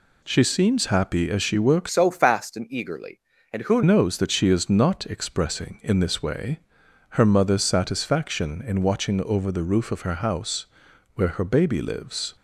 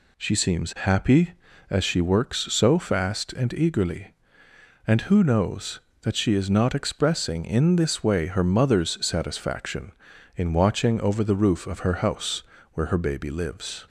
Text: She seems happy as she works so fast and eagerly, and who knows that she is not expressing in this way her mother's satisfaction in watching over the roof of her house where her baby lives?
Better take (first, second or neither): second